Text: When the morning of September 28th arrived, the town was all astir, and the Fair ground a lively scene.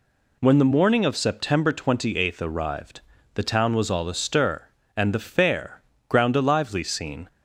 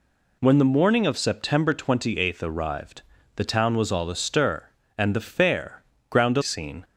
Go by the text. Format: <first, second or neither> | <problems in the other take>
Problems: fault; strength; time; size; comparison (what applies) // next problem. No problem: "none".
first | pauses between "Fair" and "ground"; slight; at 5.8 s; 0.28 s long; slight in the first // skips "lively"; at 6.4 s